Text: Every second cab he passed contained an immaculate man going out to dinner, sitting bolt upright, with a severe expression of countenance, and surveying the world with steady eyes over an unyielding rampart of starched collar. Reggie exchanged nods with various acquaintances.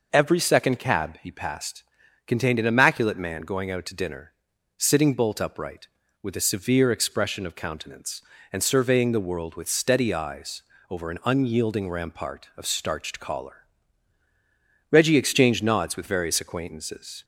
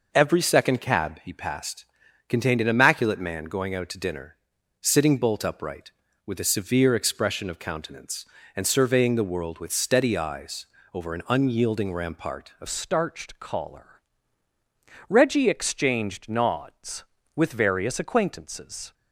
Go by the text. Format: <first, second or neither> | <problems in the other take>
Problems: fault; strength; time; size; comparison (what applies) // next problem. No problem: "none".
first | pauses between "passed" and "contained"; at 1.8 s; 0.42 s long; also in the first // pauses between "eyes" and "over"; slight; at 10.6 s; 0.28 s long; slight in the first // changes voice at "starched"; from 12.6 s on; 6.3 s long